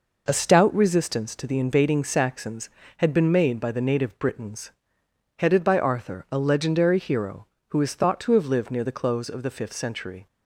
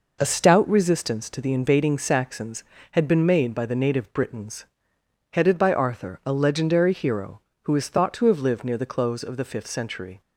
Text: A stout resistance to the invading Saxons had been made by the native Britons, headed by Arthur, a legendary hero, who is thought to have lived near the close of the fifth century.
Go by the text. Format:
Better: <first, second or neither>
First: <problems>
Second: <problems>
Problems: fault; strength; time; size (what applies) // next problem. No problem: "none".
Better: neither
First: none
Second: none